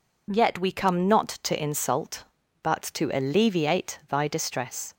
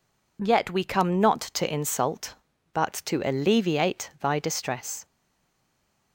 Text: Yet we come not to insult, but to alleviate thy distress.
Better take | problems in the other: first | stays silent after the last word; from 5.0 s on; 1.1 s long

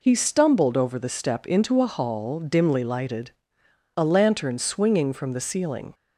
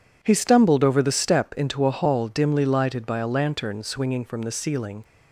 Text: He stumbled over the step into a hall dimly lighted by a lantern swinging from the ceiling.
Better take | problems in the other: second | skips "by"; at 3.6 s

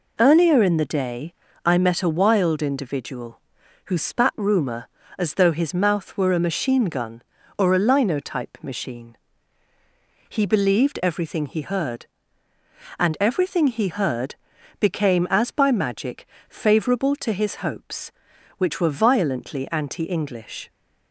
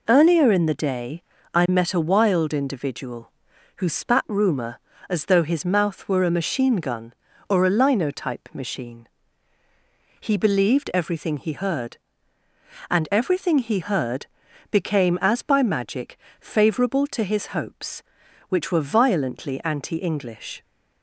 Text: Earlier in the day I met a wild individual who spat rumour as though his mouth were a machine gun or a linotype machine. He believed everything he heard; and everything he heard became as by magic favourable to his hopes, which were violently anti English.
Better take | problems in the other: neither | pauses between "day" and "I"; slight; the same in both // pauses between "heard" and "became"; the same in both // pauses between "magic" and "favourable"; slight; the same in both

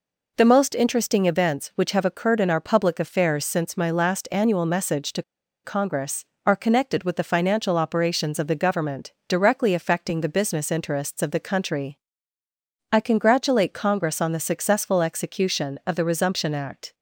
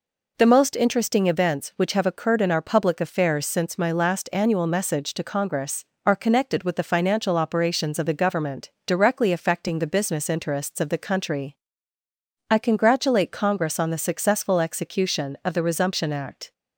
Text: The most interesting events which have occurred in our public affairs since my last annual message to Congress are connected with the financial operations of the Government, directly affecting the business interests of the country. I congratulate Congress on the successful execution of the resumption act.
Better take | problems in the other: second | pauses between "to" and "Congress"; at 5.2 s; 0.42 s long

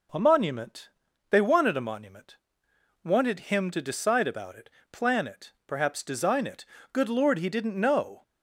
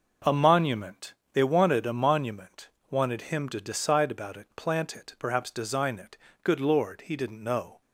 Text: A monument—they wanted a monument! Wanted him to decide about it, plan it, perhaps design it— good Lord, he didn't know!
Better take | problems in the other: first | says "plant" for "plan"; at 4.5 s

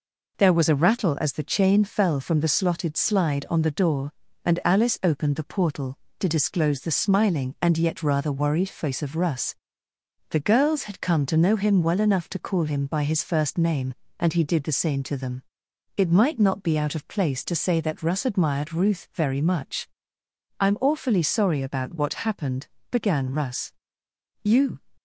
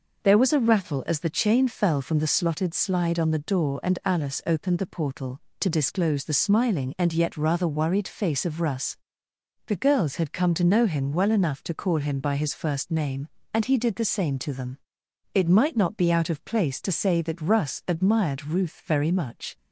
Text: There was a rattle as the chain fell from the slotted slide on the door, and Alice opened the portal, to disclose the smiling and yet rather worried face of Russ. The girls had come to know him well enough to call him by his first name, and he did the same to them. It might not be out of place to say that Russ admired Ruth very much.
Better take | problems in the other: second | goes on to say "I'm awfully sorry about what happened began Russ You"; strong; from 20.5 s on; 4.2 s long

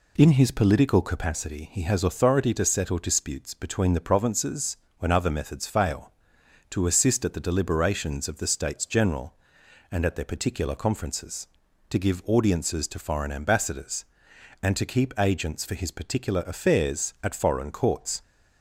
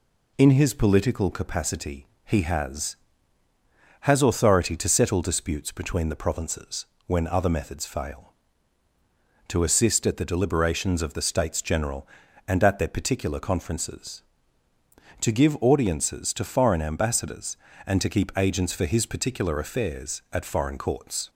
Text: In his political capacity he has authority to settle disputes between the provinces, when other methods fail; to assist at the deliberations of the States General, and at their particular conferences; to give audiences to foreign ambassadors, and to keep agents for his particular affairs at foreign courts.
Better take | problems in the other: first | pauses between "capacity" and "he"; slight; at 2.0 s; 0.18 s long // says "has" twice; at 3.9 s

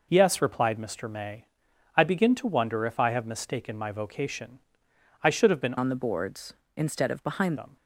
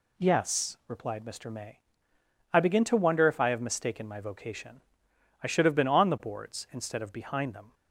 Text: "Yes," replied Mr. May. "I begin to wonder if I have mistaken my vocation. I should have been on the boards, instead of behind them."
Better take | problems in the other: second | changes voice from "on" to "behind"; from 5.7 to 7.5 s; 1.8 s long

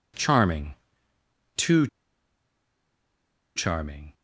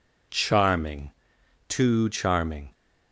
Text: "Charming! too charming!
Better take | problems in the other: second | pauses between "too" and "charming"; strong; at 1.8 s; 1.6 s long

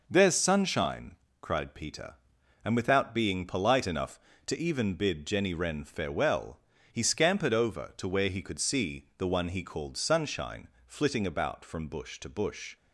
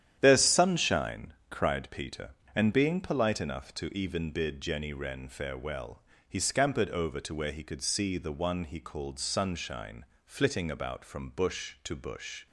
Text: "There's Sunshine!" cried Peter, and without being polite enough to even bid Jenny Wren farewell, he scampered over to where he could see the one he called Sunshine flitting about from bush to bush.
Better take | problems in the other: first | starts louder than the rest; strong; until 1.2 s; 10 dB // skips "without"; at 2.7 s // pauses between "Sunshine" and "flitting"; slight; at 10.0 s; 0.22 s long; slight in the first

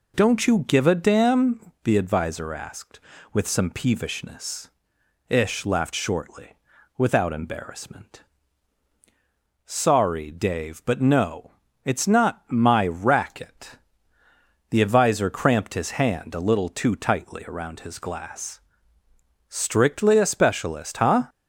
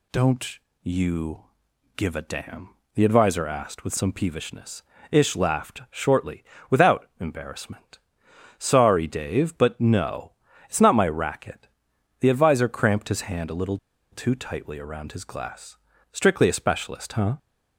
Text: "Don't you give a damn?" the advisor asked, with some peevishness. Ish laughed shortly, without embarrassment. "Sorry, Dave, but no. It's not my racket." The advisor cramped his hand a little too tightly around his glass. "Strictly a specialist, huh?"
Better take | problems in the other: first | pauses between "Don't" and "you"; slight; at 0.5 s; 0.24 s long // pauses between "you" and "give"; noticeable; at 1.4 s; 0.52 s long // pauses between "little" and "too"; slight; at 13.7 s; 0.35 s long

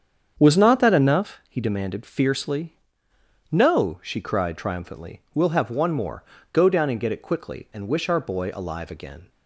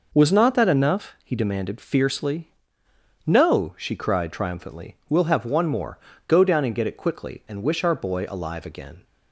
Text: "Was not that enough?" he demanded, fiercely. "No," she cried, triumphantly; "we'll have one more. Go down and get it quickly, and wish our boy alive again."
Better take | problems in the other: second | starts louder than the rest; strong; until 1.2 s; 7.5 dB

